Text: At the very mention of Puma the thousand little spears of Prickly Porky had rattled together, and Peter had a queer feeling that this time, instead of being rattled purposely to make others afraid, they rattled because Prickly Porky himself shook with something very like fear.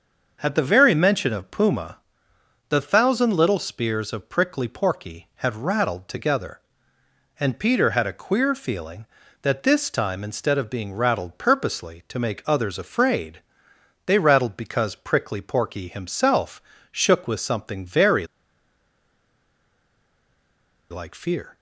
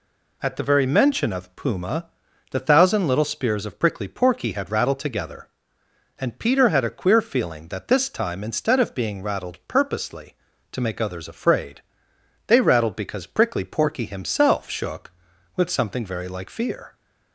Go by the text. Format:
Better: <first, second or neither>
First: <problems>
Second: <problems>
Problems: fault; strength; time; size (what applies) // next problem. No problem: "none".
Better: second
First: starts louder than the rest; until 1.4 s; 6.5 dB // pauses between "Puma" and "the"; noticeable; at 1.9 s; 0.72 s long // pauses between "himself" and "shook"; slight; at 16.6 s; 0.30 s long // pauses between "very" and "like"; strong; at 18.2 s; 2.6 s long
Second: pauses between "Puma" and "the"; at 2.0 s; 0.44 s long